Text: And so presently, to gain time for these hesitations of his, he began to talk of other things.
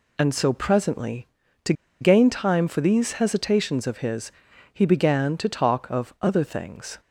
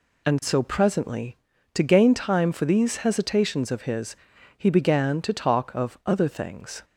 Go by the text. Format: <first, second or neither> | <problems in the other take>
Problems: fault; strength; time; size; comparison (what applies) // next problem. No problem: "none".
second | pauses between "to" and "gain"; slight; at 1.7 s; 0.28 s long